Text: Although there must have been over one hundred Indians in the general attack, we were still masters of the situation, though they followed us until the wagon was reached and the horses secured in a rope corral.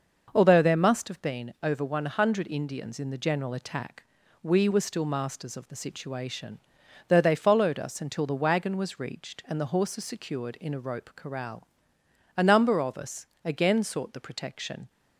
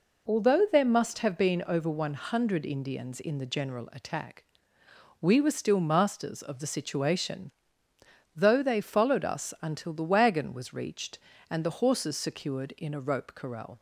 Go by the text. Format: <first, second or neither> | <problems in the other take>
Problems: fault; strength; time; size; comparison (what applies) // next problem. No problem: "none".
second | starts louder than the rest; until 1.3 s; 6 dB // goes on to say "A number of us again sought the protection"; strong; from 12.3 s on; 2.5 s long